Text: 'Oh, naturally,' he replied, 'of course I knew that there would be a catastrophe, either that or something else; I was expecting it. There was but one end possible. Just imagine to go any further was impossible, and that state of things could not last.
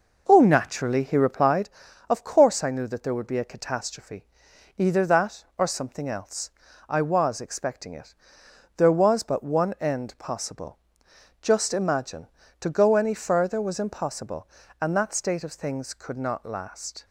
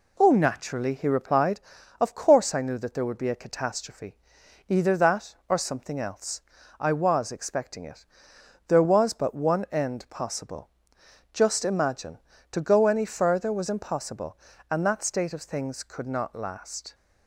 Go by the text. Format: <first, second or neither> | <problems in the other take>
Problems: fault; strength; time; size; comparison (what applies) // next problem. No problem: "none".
second | starts louder than the rest; noticeable; until 1.5 s; 5.5 dB